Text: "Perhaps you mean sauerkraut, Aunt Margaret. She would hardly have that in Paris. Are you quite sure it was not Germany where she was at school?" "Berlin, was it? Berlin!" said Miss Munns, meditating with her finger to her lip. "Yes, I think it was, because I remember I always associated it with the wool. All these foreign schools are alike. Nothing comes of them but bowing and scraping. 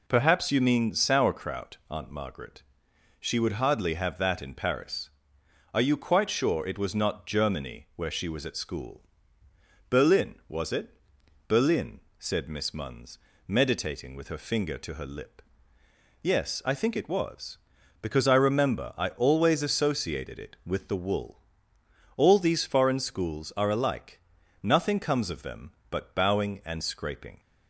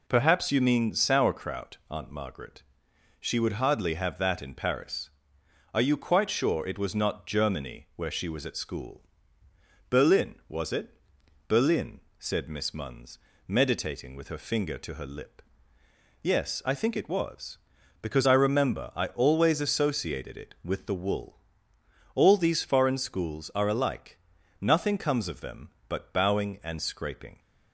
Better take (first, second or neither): neither